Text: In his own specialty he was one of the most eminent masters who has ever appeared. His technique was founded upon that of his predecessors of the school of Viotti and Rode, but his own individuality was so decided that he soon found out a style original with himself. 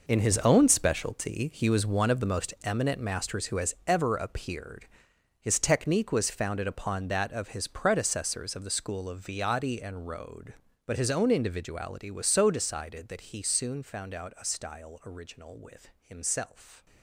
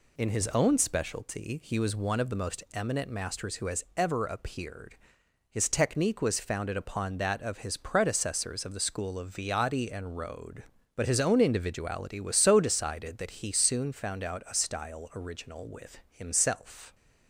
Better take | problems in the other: second | gets quieter; strong; throughout; 13 dB

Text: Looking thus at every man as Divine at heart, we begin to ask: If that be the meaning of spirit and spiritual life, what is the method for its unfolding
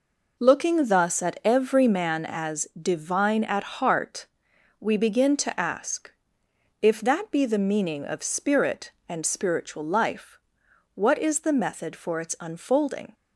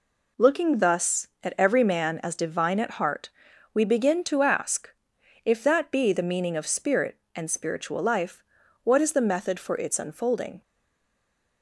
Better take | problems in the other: first | stays silent after the last word; from 10.6 s on; 1.0 s long

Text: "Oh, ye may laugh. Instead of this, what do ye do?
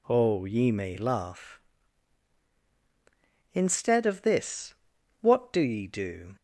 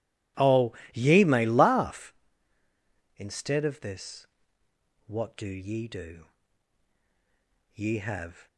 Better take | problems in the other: first | goes on to say "Ye have"; noticeable; from 7.7 s on; 0.72 s long

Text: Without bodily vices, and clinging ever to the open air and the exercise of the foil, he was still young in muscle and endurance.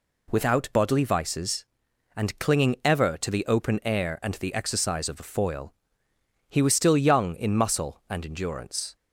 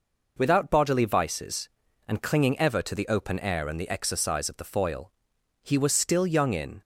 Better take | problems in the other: first | stops before "muscle and endurance"; at 6.8 s

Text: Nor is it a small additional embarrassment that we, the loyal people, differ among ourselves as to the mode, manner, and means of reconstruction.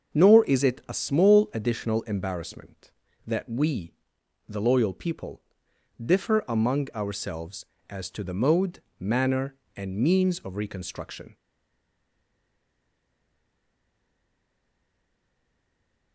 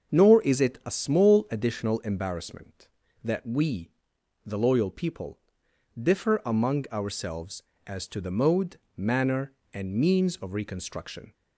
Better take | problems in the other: second | starts louder than the rest; until 1.2 s; 6.5 dB; also in the second // stays silent after the last word; strong; from 11.3 s on; 4.8 s long

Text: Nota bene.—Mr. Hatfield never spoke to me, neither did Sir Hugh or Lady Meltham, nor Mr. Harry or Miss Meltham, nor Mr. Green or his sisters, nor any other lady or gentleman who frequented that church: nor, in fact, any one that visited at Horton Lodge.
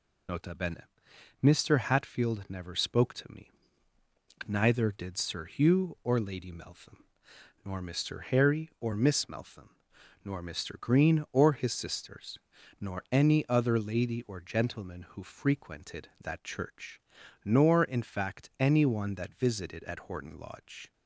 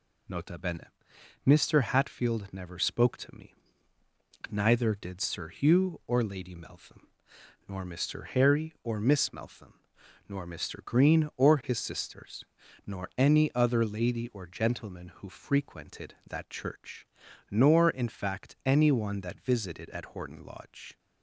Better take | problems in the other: second | loses the start of "Nota"; at 0.2 s; 35 ms

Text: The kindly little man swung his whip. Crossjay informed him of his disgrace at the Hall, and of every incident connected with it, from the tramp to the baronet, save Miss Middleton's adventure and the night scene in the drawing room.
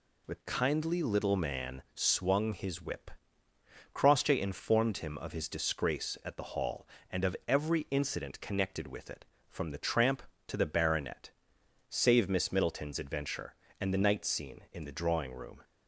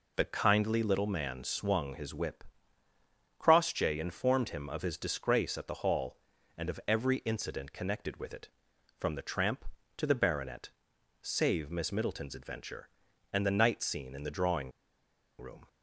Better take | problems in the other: first | pauses between "drawing" and "room"; noticeable; at 14.7 s; 0.68 s long

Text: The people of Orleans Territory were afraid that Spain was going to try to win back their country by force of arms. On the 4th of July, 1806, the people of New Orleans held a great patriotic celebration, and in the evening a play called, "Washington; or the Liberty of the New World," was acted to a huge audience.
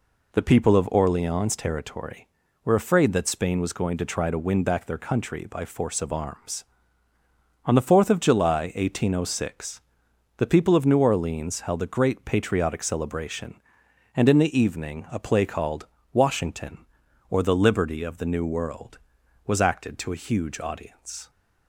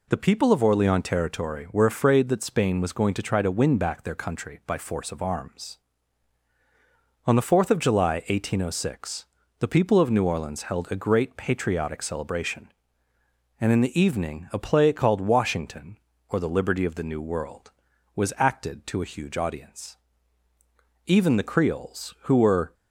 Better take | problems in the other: first | goes on to say "Even the Creoles who were"; strong; from 21.0 s on; 1.6 s long

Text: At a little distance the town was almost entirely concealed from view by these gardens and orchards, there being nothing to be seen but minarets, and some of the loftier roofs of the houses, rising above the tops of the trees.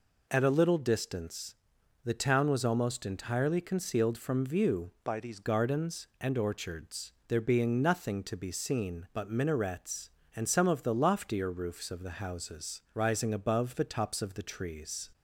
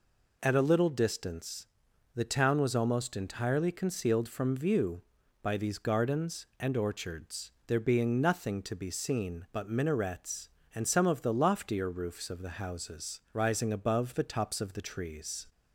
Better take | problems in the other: second | pauses between "distance" and "the"; noticeable; at 1.5 s; 0.48 s long; noticeable in the second // changes voice from "by" to "these"; from 5.0 to 5.4 s; 0.4 s long

